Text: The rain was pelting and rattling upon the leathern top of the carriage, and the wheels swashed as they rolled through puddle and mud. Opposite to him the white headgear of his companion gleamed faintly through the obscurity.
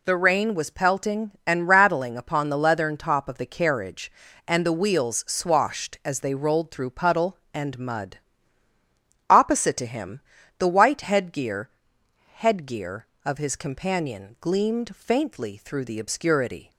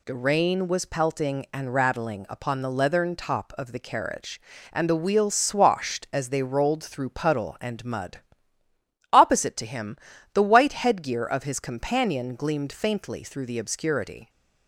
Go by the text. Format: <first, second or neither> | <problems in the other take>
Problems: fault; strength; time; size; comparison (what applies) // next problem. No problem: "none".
second | pauses between "him" and "the"; slight; at 10.2 s; 0.36 s long; slight in the second // says "headgear" twice; at 12.3 s